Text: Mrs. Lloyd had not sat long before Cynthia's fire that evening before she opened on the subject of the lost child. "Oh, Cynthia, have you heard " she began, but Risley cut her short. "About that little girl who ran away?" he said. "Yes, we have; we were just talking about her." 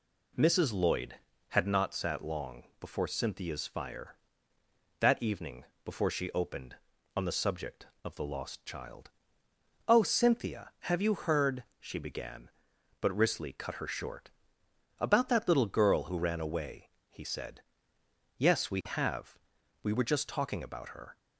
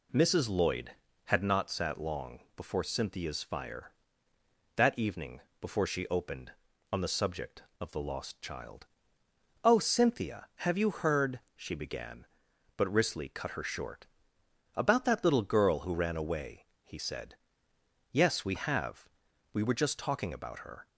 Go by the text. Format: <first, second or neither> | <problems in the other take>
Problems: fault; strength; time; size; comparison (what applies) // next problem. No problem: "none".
neither | pauses between "long" and "before"; slight; the same in both // pauses between "evening" and "before"; slight; the same in both